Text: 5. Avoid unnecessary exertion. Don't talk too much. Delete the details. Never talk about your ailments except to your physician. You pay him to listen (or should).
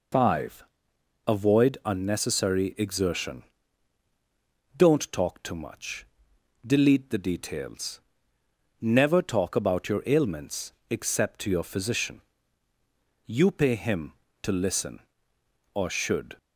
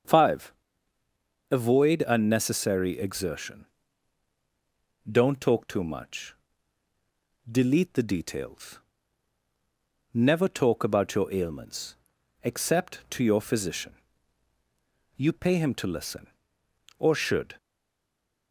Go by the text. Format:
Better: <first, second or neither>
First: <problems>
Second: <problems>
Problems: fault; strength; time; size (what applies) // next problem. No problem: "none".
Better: first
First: pauses between "ailments" and "except"; slight; at 10.7 s; 0.20 s long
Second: starts louder than the rest; until 2.0 s; 6.5 dB // pauses between "ailments" and "except"; noticeable; at 11.9 s; 0.48 s long // stays silent after the last word; slight; from 17.5 s on; 1.0 s long